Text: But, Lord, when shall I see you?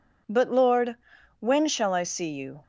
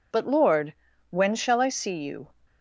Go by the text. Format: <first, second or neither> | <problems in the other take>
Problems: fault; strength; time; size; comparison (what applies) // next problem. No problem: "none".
neither | none